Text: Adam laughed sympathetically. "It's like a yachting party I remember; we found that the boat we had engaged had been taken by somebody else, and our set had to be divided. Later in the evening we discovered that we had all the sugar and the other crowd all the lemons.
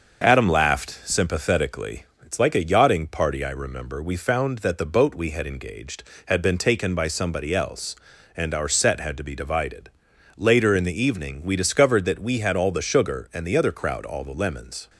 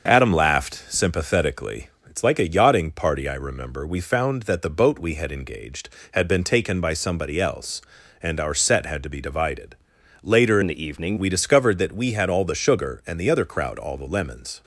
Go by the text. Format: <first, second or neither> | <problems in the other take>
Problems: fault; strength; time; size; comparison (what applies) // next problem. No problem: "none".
first | starts louder than the rest; until 1.1 s; 6.5 dB; also in the first // changes voice from "in" to "evening"; from 10.6 to 11.1 s; 0.5 s long